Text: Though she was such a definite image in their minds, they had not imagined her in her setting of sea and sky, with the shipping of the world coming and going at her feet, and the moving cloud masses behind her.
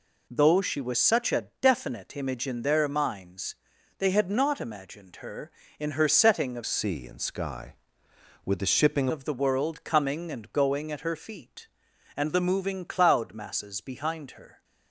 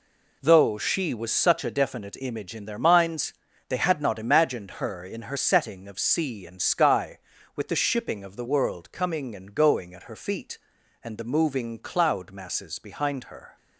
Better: second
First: changes voice from "sea" to "shipping"; from 6.6 to 9.0 s; 2.4 s long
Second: none

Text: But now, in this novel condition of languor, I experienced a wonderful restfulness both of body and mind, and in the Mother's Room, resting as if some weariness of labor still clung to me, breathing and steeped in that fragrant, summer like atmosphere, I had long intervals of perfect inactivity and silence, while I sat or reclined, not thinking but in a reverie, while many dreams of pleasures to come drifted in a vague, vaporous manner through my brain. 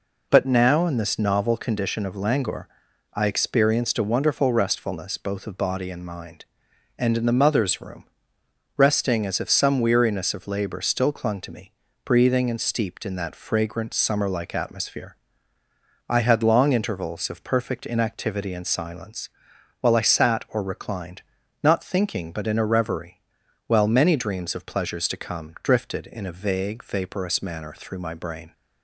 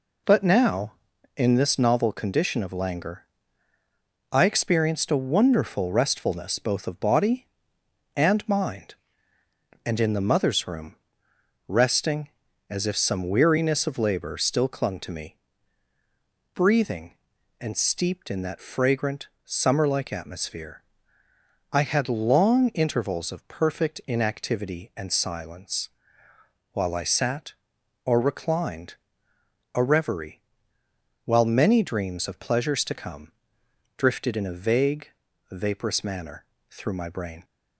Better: first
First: none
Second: skips "not thinking but in"; at 29.3 s // pauses between "come" and "drifted"; noticeable; at 33.3 s; 0.64 s long // pauses between "manner" and "through"; slight; at 36.4 s; 0.24 s long

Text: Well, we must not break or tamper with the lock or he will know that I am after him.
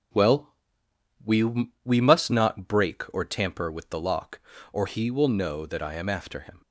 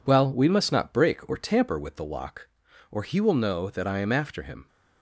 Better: second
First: says "we" twice; at 1.8 s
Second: none

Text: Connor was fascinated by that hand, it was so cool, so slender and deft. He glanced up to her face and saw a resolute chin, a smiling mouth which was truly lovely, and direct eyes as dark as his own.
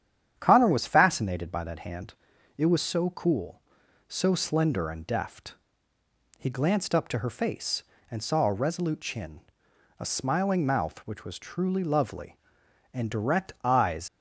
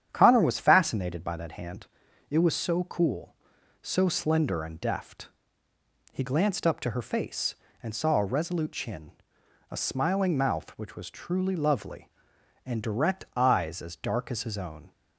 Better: second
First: starts louder than the rest; strong; until 1.3 s; 9.5 dB // stops before "as dark as his own"; at 14.0 s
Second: starts louder than the rest; strong; until 1.1 s; 9.5 dB

